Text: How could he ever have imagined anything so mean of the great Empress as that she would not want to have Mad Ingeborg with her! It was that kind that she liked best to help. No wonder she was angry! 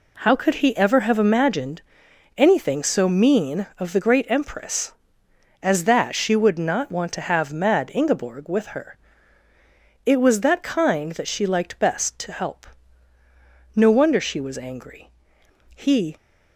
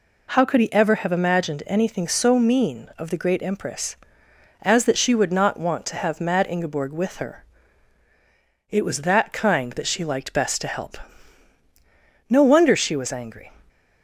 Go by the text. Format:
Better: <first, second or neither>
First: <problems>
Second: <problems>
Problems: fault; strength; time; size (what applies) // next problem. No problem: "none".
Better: second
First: pauses between "imagined" and "anything"; noticeable; at 1.8 s; 0.56 s long // goes on to say "He"; slight; from 15.7 s on; 0.40 s long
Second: none